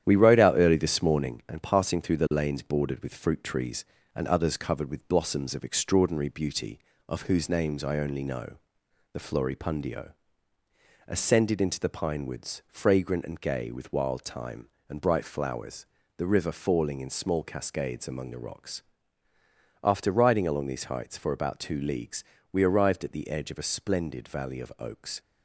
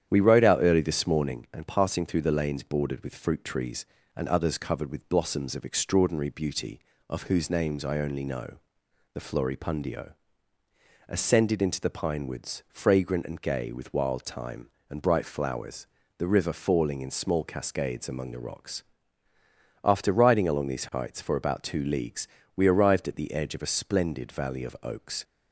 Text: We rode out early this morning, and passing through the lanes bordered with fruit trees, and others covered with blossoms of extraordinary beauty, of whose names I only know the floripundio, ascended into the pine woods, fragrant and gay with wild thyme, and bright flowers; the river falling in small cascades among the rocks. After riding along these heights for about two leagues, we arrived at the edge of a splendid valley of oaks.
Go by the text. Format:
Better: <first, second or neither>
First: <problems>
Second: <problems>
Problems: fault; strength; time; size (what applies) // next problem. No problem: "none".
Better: second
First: gets quieter; noticeable; throughout; 5.5 dB // starts louder than the rest; strong; until 1.0 s; 10 dB // pauses between "know" and "the"; noticeable; at 8.5 s; 0.60 s long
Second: starts louder than the rest; strong; until 1.1 s; 9.5 dB // pauses between "know" and "the"; noticeable; at 8.5 s; 0.60 s long